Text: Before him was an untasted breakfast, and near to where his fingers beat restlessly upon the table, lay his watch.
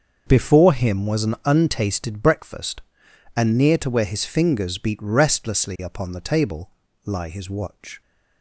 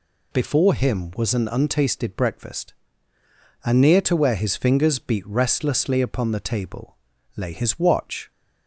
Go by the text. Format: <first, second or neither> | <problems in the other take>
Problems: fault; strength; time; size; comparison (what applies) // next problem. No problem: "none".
second | starts louder than the rest; until 1.2 s; 6.5 dB // says "lie" for "lay"; at 7.0 s